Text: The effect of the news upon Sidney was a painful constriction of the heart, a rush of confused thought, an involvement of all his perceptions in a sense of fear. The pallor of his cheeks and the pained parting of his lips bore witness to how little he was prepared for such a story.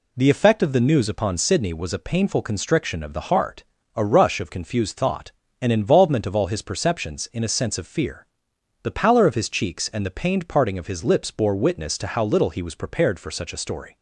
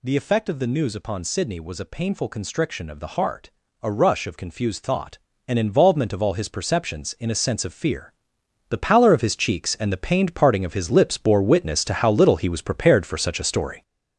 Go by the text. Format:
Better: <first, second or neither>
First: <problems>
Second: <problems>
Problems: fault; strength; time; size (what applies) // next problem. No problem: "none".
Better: first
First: none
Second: gets louder; strong; throughout; 7 dB